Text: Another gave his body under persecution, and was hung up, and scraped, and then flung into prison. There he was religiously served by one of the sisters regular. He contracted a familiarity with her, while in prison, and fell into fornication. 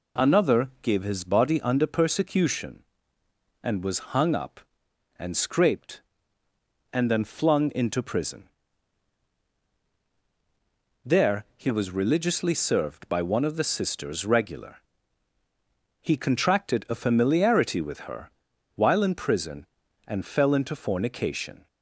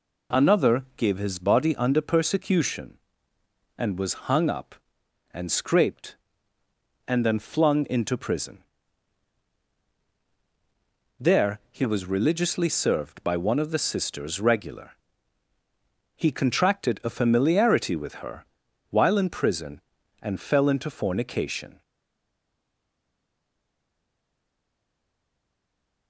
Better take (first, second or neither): first